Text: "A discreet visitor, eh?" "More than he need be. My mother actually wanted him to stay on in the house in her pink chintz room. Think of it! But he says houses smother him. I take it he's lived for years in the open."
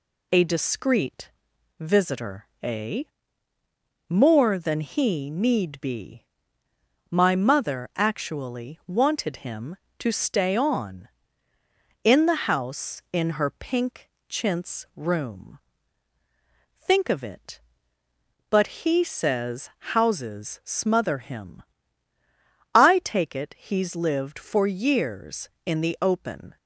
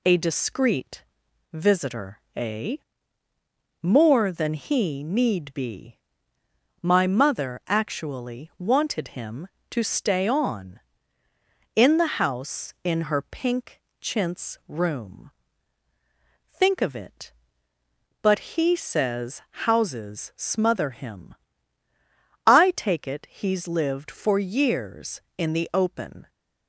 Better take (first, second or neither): neither